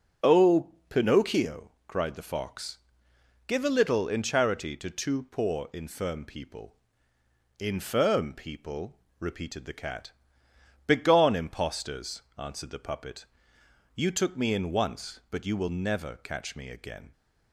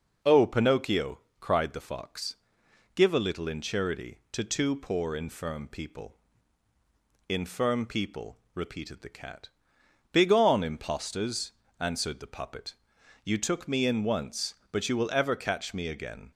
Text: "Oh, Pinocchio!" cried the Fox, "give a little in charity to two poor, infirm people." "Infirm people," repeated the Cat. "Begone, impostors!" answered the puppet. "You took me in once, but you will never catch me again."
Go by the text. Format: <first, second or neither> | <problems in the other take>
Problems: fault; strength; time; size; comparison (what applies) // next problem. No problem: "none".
first | says "ever" for "never"; at 15.1 s